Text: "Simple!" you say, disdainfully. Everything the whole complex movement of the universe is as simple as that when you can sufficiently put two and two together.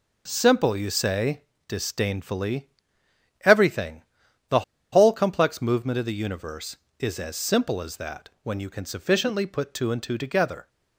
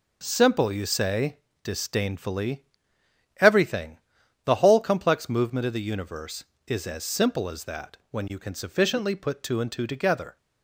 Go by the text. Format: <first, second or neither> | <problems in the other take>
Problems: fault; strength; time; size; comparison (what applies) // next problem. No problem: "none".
second | pauses between "Everything" and "the"; noticeable; at 4.0 s; 0.46 s long; noticeable in the second // pauses between "the" and "whole"; slight; at 4.6 s; 0.30 s long // pauses between "that" and "when"; slight; at 8.2 s; 0.16 s long; slight in the second